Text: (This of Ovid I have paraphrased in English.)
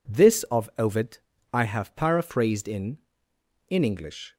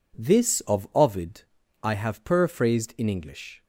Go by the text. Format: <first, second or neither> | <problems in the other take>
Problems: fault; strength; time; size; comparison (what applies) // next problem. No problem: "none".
second | pauses between "Ovid" and "I"; slight; at 1.1 s; 0.34 s long; also in the second // says "in" twice; at 3.6 s